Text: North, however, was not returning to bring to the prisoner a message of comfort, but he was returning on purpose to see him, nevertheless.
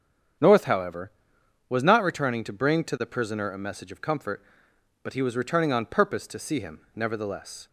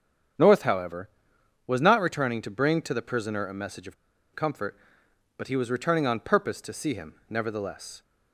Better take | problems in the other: first | starts louder than the rest; strong; until 1.9 s; 8 dB; strong in the first // pauses between "of" and "comfort"; at 3.9 s; 0.41 s long

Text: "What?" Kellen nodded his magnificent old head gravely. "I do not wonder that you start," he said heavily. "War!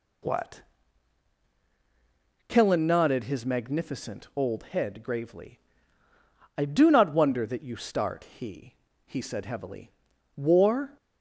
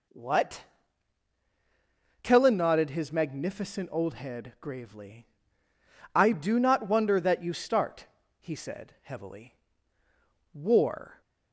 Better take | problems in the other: second | says "he" twice; at 9.0 s

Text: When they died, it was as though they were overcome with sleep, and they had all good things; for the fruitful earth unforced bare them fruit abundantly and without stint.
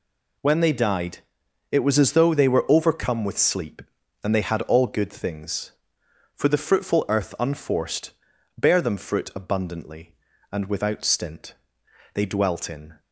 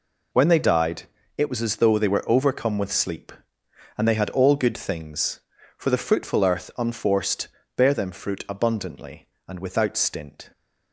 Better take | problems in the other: second | pauses between "unforced" and "bare"; at 8.1 s; 0.44 s long; slight in the second // goes on to say "They dwelt in"; noticeable; from 12.1 s on; 0.86 s long

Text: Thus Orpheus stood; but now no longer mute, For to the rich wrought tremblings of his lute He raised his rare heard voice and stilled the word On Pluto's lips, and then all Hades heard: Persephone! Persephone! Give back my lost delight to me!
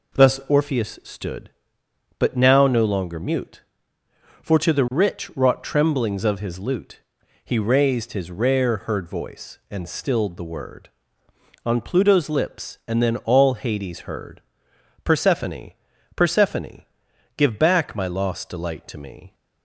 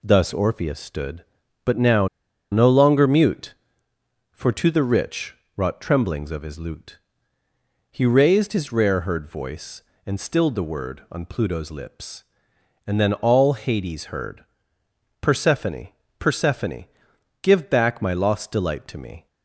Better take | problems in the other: first | pauses between "now" and "no"; at 2.0 s; 0.44 s long // pauses between "rich" and "wrought"; slight; at 5.3 s; 0.18 s long // pauses between "lute" and "He"; noticeable; at 6.9 s; 0.94 s long; also in the first

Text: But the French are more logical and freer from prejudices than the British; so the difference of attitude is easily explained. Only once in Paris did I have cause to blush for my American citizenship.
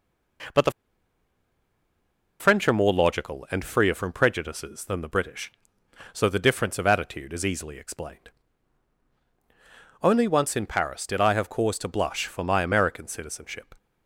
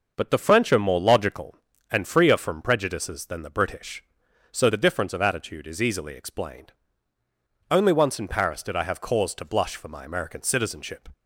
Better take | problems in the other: second | pauses between "the" and "French"; strong; at 0.7 s; 1.6 s long

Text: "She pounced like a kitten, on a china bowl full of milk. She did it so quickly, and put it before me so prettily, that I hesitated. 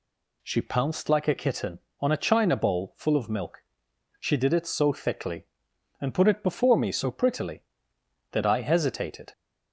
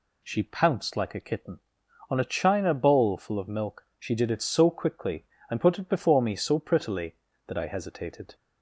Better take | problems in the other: second | says "thickly" for "quickly"; at 4.9 s

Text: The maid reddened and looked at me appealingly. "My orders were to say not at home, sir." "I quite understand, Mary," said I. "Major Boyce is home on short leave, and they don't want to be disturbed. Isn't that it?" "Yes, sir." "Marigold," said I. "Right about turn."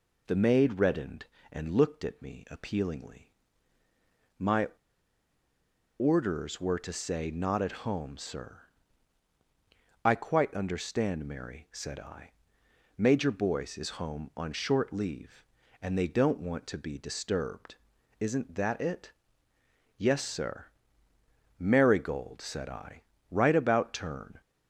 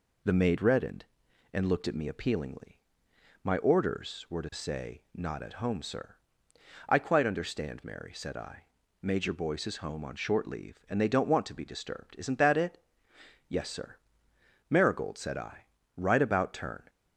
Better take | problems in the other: second | pauses between "My" and "orders"; strong; at 4.6 s; 1.3 s long

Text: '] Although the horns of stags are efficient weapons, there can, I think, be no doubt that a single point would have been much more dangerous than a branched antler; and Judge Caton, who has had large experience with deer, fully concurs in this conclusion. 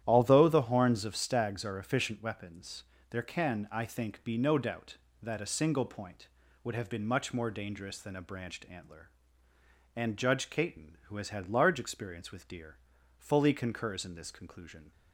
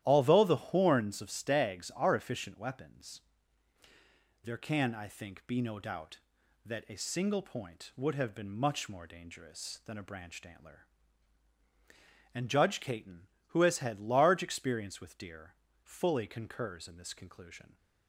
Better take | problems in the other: neither | starts louder than the rest; strong; the same in both

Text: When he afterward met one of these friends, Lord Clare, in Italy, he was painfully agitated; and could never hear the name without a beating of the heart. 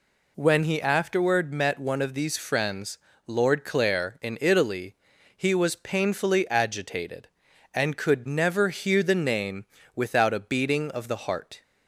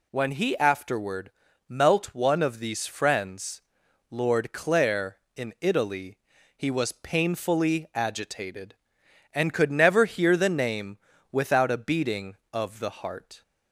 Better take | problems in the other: first | says "melt" for "met"; at 1.6 s // pauses between "name" and "without"; slight; at 10.9 s; 0.34 s long; slight in the first

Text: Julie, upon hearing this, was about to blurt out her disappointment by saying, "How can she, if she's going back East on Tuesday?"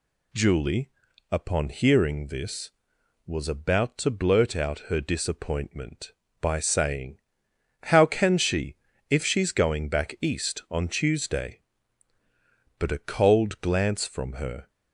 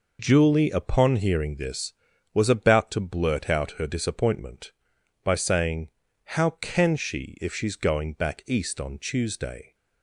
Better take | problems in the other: second | goes on to say "But a cold glance from her"; strong; from 12.7 s on; 1.9 s long

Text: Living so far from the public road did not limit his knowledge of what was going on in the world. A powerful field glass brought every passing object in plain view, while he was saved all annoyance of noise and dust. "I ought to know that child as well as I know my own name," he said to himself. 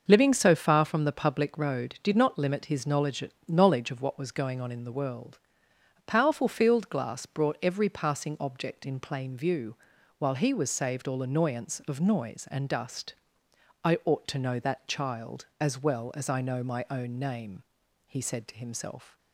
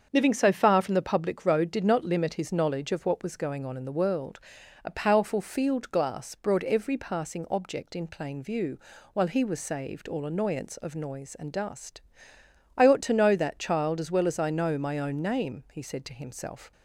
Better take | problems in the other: second | starts louder than the rest; noticeable; until 1.0 s; 6 dB; also in the second // says "knowledge" twice; at 3.4 s

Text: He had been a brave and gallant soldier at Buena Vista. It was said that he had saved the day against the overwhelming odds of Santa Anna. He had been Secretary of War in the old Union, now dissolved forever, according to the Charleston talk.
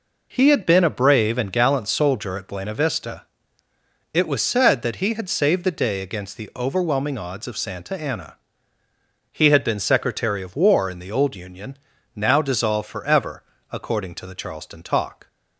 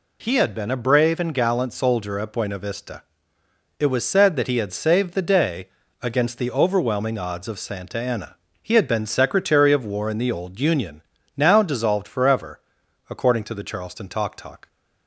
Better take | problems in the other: first | pauses between "day" and "against"; slight; at 5.6 s; 0.30 s long // says "talk" twice; at 14.3 s

